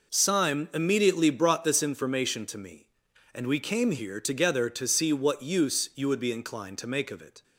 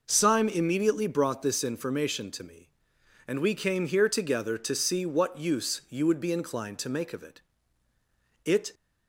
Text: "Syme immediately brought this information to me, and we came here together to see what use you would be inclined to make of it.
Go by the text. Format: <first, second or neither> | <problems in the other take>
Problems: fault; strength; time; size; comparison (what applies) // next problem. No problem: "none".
first | goes on to say "It"; slight; from 8.4 s on; 0.30 s long